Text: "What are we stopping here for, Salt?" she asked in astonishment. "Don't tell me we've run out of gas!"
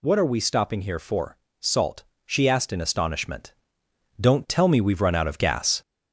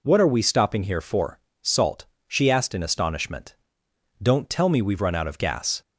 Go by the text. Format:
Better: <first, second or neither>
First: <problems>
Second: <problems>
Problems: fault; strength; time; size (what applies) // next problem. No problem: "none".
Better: second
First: gets louder; slight; throughout; 3.5 dB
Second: none